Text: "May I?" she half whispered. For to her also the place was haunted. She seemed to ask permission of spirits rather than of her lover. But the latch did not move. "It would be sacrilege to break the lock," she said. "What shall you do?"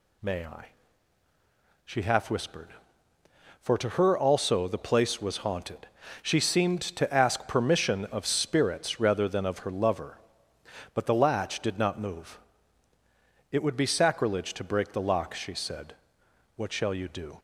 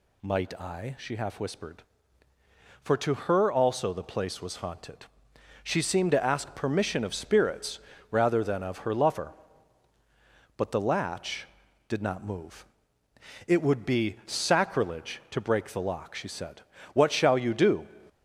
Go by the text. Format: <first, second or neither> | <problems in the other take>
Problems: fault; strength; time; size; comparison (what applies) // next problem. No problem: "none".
first | says "Might" for "May"; at 0.2 s // pauses between "spirits" and "rather"; slight; at 7.7 s; 0.30 s long